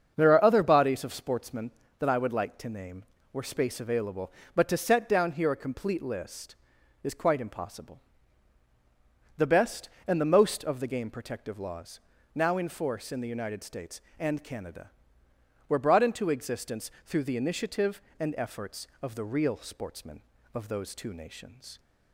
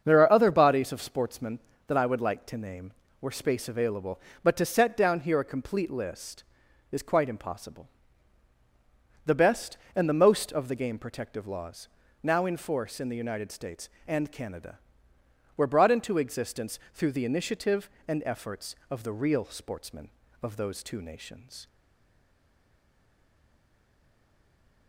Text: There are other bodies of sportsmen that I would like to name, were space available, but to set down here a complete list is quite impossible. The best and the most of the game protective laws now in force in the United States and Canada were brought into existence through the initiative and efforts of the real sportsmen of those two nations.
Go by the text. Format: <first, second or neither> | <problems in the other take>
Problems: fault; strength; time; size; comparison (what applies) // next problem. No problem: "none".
first | starts louder than the rest; until 1.0 s; 7 dB; also in the first // pauses between "laws" and "now"; at 11.8 s; 0.38 s long; also in the first // stays silent after the last word; strong; from 21.6 s on; 3.2 s long